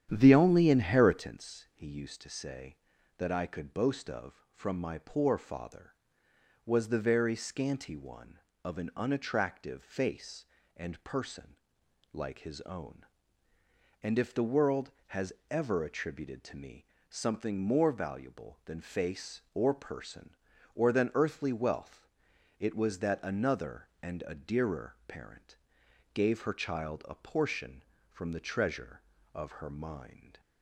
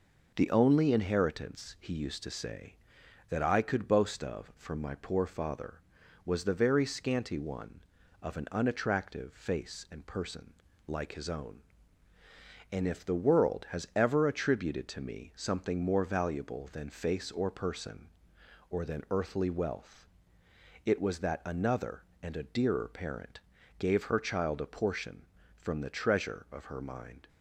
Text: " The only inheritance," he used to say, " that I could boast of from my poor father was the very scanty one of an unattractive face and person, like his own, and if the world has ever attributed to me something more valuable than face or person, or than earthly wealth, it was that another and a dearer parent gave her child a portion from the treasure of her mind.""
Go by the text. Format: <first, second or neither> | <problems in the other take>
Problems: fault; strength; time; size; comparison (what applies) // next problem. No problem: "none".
second | starts louder than the rest; strong; until 1.3 s; 9.5 dB // pauses between "has" and "ever"; slight; at 15.3 s; 0.16 s long // pauses between "me" and "something"; slight; at 16.8 s; 0.22 s long // pauses between "parent" and "gave"; noticeable; at 25.5 s; 0.58 s long; also in the second